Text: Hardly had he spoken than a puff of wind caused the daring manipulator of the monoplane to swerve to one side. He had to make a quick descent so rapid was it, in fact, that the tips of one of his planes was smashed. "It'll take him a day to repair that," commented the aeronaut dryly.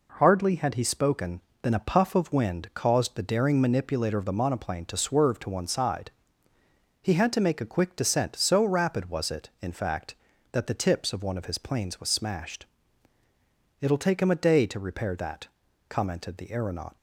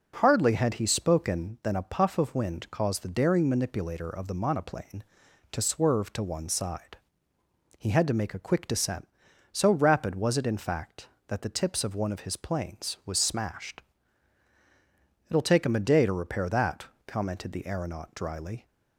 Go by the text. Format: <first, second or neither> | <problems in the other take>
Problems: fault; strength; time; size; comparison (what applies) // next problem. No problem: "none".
second | stops before "dryly"; at 16.9 s